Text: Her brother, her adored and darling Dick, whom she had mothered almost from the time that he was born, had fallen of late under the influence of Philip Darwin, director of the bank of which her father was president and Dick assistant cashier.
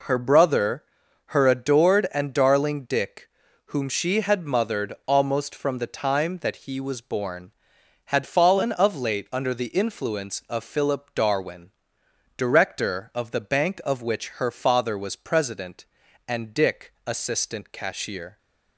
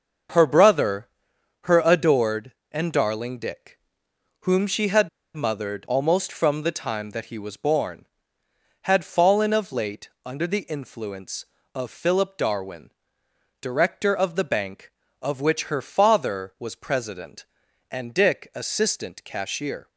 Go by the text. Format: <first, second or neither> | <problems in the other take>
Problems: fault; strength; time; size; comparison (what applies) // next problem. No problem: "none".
first | starts louder than the rest; until 1.8 s; 6 dB // pauses between "had" and "mothered"; slight; at 5.0 s; 0.26 s long // pauses between "late" and "under"; slight; at 10.0 s; 0.16 s long